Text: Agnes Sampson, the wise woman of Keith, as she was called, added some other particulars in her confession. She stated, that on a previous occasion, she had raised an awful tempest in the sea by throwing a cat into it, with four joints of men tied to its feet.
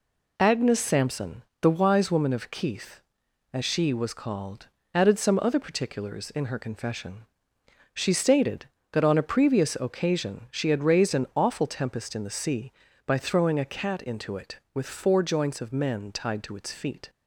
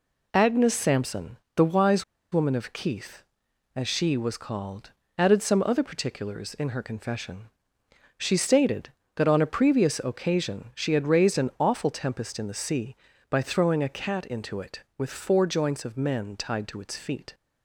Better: first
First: none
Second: pauses between "wise" and "woman"; slight; at 2.0 s; 0.30 s long

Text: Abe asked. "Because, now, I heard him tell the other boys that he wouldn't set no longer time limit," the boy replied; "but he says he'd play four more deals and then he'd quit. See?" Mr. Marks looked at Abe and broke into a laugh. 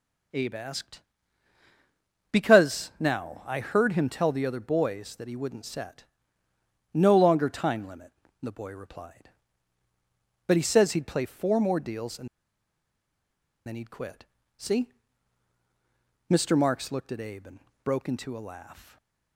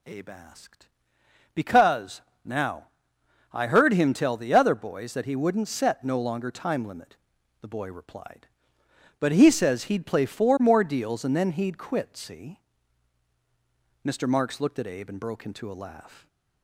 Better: second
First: pauses between "set" and "no"; noticeable; at 6.0 s; 0.90 s long // pauses between "and" and "then"; strong; at 12.2 s; 1.3 s long // pauses between "and" and "broke"; slight; at 17.5 s; 0.24 s long // stays silent after the last word; slight; from 18.7 s on; 0.6 s long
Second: none

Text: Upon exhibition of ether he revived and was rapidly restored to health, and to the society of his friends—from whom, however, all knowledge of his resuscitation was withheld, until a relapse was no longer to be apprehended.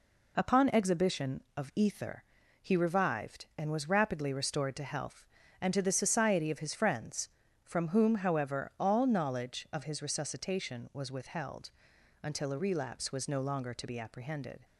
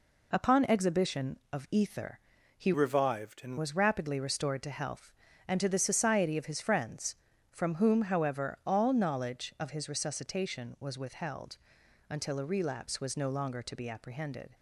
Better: first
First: pauses between "ether" and "he"; at 2.2 s; 0.38 s long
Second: pauses between "ether" and "he"; at 2.1 s; 0.38 s long // changes voice from "revived" to "and"; from 2.7 to 3.5 s; 0.8 s long

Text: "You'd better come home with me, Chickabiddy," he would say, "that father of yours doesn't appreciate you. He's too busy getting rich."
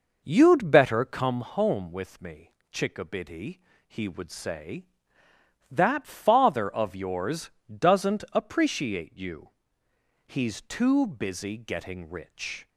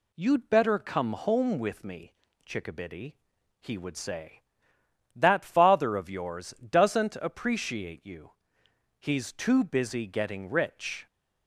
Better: second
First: starts louder than the rest; noticeable; until 1.4 s; 5.5 dB // pauses between "yours" and "doesn't"; slight; at 7.5 s; 0.18 s long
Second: none

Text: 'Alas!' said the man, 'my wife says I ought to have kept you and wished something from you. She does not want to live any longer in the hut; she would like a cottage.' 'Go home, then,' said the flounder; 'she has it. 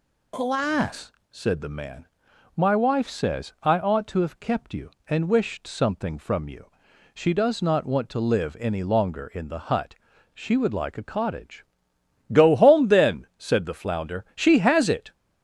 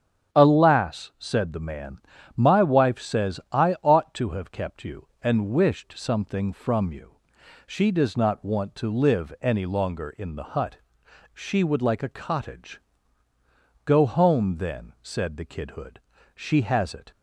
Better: first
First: none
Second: starts louder than the rest; strong; until 1.4 s; 9.5 dB // says "kidhood" for "flounder"; at 15.4 s

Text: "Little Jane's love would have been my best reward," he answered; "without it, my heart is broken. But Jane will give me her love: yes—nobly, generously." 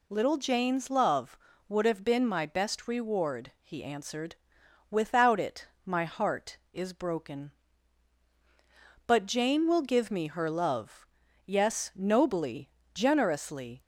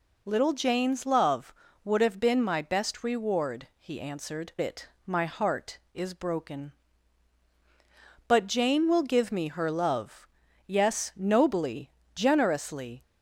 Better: first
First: none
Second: skips "without"; at 4.5 s

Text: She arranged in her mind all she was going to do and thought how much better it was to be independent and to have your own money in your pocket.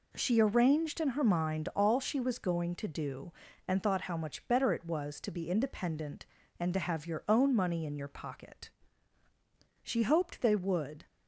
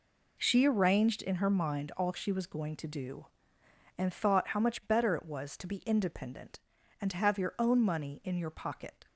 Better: second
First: goes on to say "She hoped they would"; noticeable; from 9.8 s on; 1.2 s long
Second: none

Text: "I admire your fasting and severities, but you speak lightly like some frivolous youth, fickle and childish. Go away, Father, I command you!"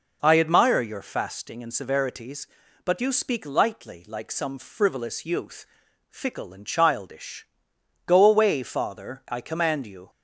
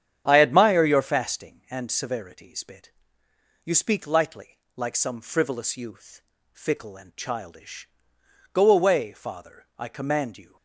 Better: first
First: none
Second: starts louder than the rest; strong; until 1.2 s; 9 dB // says "bit" for "but"; at 2.6 s // pauses between "lightly" and "like"; slight; at 4.5 s; 0.16 s long

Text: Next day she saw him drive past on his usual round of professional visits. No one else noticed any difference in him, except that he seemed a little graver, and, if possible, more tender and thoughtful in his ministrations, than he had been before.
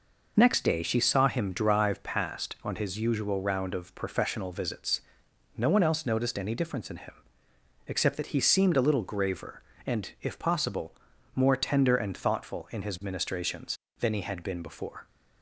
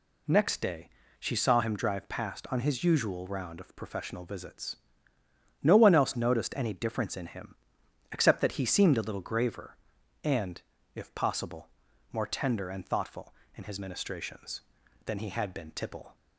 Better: first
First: none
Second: pauses between "day" and "she"; slight; at 0.8 s; 0.30 s long // says "tipple" for "before"; at 15.7 s

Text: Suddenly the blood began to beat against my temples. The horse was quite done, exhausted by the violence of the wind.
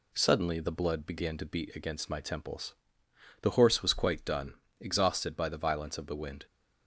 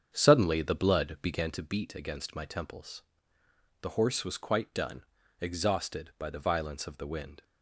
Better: first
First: none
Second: starts louder than the rest; strong; until 1.6 s; 7.5 dB

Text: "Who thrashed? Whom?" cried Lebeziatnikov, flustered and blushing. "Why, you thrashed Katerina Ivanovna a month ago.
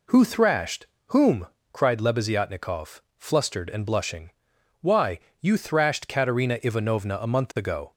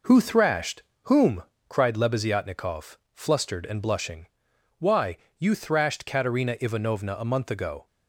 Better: first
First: none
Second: gets quieter; noticeable; throughout; 5 dB

